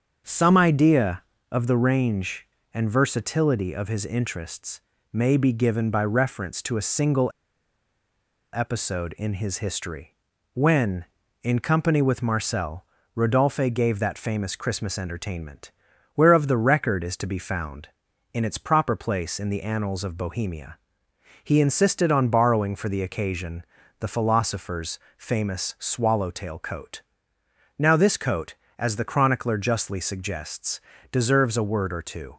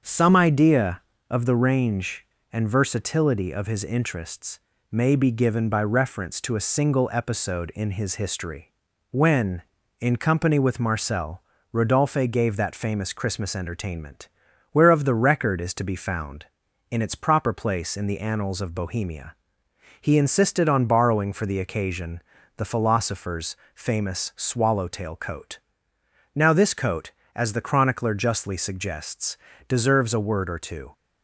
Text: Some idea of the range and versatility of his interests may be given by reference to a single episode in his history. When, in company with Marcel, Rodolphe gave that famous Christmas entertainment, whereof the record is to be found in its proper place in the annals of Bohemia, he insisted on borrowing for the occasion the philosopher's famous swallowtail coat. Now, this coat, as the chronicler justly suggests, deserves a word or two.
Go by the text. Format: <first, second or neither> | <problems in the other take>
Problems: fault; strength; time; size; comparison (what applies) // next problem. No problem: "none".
second | starts louder than the rest; until 1.5 s; 7 dB; also in the second // pauses between "interests" and "may"; slight; at 4.8 s; 0.32 s long; slight in the second // pauses between "single" and "episode"; at 7.2 s; 1.2 s long // pauses between "occasion" and "the"; at 23.6 s; 0.38 s long; also in the second // pauses between "philosopher's" and "famous"; slight; at 24.9 s; 0.18 s long; slight in the second